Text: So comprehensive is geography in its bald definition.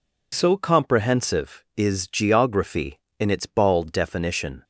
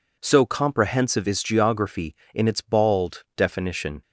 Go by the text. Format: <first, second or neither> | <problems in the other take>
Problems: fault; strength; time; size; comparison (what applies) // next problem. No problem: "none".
neither | none